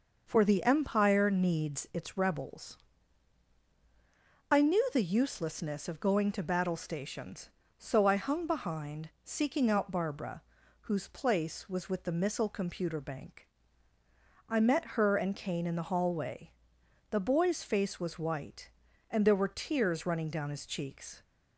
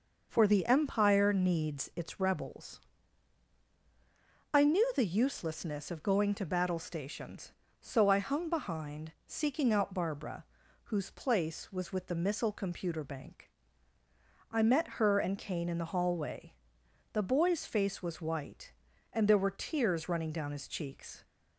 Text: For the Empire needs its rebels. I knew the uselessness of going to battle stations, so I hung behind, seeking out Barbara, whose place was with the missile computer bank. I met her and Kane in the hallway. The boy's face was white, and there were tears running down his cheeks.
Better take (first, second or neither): neither